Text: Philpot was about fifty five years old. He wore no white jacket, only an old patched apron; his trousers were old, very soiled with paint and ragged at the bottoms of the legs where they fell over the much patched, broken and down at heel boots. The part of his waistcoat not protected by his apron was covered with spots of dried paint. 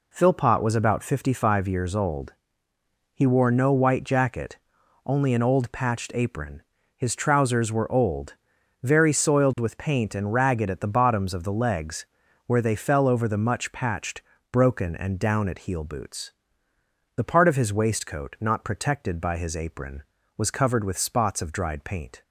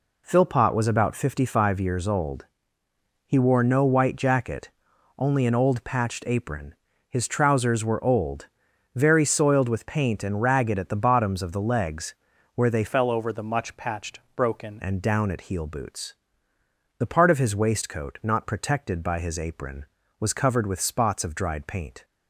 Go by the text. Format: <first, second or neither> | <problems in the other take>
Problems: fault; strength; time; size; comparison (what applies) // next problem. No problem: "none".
first | pauses between "legs" and "where"; at 12.1 s; 0.40 s long; also in the first // changes voice from "fell" to "broken"; from 12.8 to 14.7 s; 1.9 s long